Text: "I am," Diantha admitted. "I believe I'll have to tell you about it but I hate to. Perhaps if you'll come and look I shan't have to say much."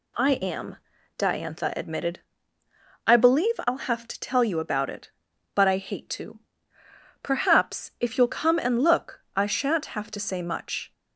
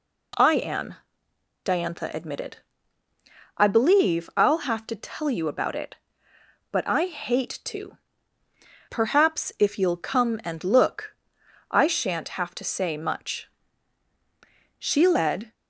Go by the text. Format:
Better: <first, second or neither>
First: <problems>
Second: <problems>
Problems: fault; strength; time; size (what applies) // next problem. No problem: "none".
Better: first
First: none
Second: pauses between "look" and "I"; noticeable; at 11.1 s; 0.56 s long // goes on to say "She led"; noticeable; from 14.8 s on; 0.72 s long